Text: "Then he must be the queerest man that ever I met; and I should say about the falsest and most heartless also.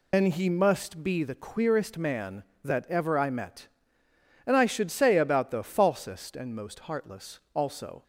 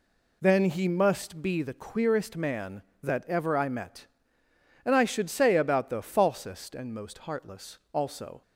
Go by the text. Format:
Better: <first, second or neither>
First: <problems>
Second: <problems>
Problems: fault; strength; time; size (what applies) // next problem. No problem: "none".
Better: second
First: loses the start of "Then"; at 0.1 s; 105 ms // pauses between "heartless" and "also"; slight; at 7.3 s; 0.16 s long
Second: pauses between "heartless" and "also"; slight; at 7.7 s; 0.16 s long